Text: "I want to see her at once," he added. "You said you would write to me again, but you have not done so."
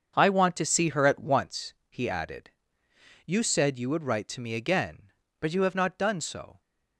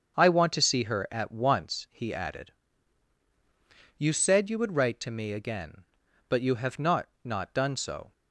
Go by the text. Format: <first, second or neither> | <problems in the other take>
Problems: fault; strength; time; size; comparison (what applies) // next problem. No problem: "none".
first | starts louder than the rest; until 1.1 s; 6.5 dB; also in the first // says "not" twice; at 7.2 s